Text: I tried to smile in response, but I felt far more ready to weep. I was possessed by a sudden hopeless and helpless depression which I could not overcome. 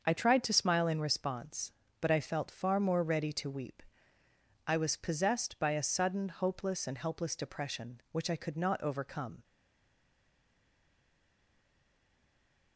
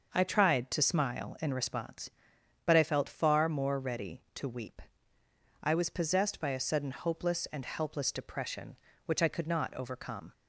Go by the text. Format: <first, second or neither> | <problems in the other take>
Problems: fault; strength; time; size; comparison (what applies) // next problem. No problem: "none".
second | starts louder than the rest; until 1.0 s; 6.5 dB; noticeable in the second // stays silent after the last word; strong; from 9.4 s on; 3.3 s long